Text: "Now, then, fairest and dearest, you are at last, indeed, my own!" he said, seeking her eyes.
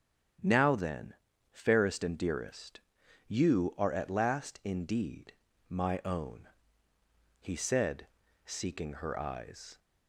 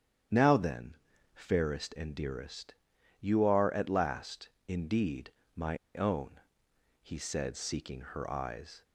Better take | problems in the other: first | starts louder than the rest; strong; until 1.7 s; 9 dB; strong in the first // pauses between "my" and "own"; slight; at 5.7 s; 0.17 s long

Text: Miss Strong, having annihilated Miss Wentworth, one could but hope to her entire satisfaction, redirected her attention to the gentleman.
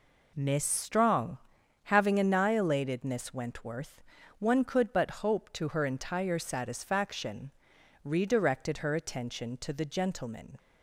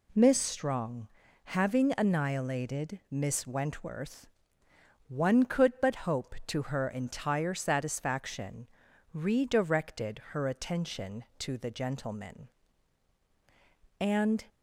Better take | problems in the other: first | goes on to say "And"; slight; from 14.0 s on; 0.44 s long

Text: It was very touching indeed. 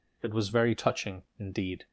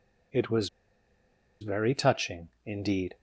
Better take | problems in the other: first | pauses between "was" and "very"; noticeable; at 0.6 s; 0.93 s long // pauses between "touching" and "indeed"; slight; at 2.4 s; 0.16 s long

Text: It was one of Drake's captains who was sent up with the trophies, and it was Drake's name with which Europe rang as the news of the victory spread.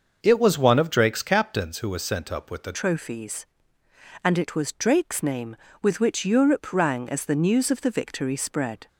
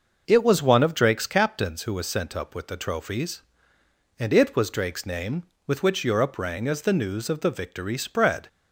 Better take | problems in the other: second | starts louder than the rest; until 1.2 s; 6.5 dB // changes voice at "trophies"; from 2.7 s on; 6.1 s long

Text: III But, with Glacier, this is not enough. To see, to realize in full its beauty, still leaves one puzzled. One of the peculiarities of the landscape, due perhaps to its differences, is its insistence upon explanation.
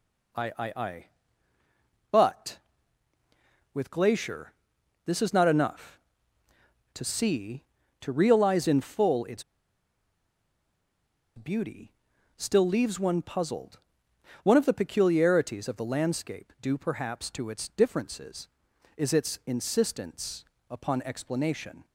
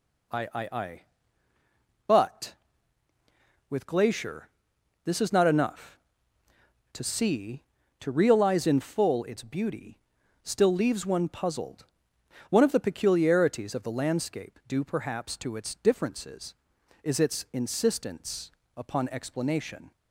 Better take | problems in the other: second | pauses between "its" and "beauty"; strong; at 9.4 s; 1.9 s long // pauses between "insistence" and "upon"; slight; at 20.4 s; 0.24 s long; slight in the second

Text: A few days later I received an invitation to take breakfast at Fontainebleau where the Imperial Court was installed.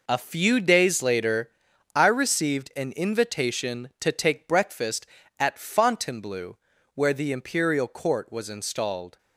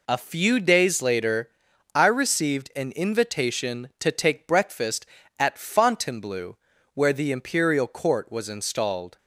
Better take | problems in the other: second | gets quieter; strong; throughout; 10 dB // pauses between "later" and "I"; noticeable; at 1.4 s; 0.46 s long; noticeable in the second // pauses between "Fontainebleau" and "where"; slight; at 6.5 s; 0.36 s long; slight in the second

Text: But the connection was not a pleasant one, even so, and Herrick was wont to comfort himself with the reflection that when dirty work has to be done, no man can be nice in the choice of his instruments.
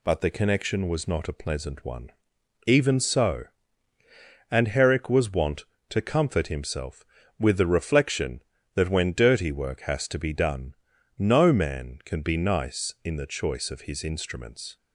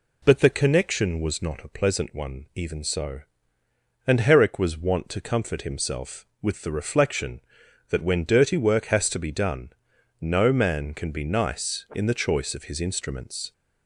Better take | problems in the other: neither | none

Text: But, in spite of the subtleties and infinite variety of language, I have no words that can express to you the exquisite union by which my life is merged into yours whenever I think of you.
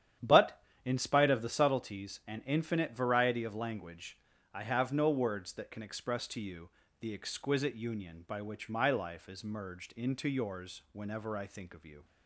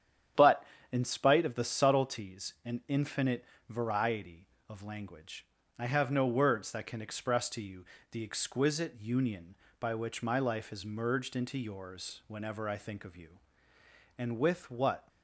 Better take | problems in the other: first | starts louder than the rest; strong; until 1.6 s; 9 dB; strong in the first // pauses between "infinite" and "variety"; slight; at 3.4 s; 0.24 s long // pauses between "you" and "the"; slight; at 7.8 s; 0.28 s long; slight in the first // goes on to say "And with what"; noticeable; from 14.1 s on; 0.90 s long

